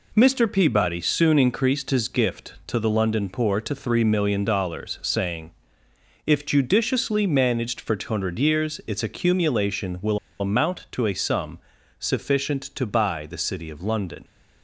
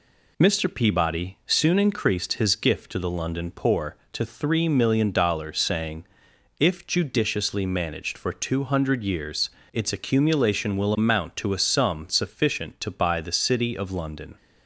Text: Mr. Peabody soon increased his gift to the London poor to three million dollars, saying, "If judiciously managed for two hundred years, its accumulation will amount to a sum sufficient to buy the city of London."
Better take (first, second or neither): second